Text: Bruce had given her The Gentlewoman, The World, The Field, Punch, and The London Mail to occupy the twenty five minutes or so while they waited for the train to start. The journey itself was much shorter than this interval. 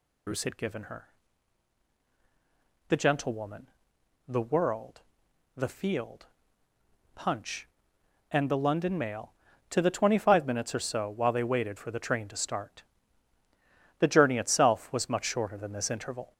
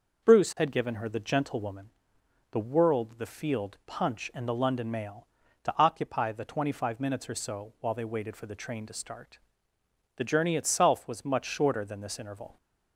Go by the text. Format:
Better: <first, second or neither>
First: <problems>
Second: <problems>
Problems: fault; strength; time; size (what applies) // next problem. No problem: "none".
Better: second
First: pauses between "her" and "The"; strong; at 1.0 s; 1.8 s long // skips "occupy"; at 9.7 s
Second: none